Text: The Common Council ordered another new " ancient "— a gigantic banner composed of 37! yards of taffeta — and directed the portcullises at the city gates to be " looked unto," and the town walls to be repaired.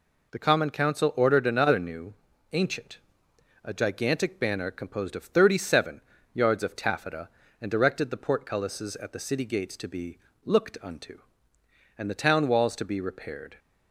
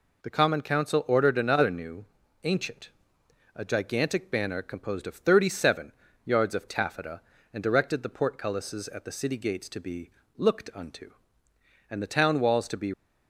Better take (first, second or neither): first